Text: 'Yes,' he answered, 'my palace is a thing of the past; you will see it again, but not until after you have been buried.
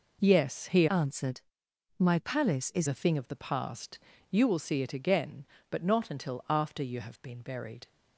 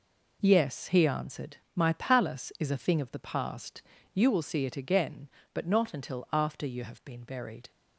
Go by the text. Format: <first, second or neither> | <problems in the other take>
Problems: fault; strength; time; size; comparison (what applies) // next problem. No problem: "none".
second | changes voice from "answered" to "is"; from 0.8 to 2.8 s; 2.0 s long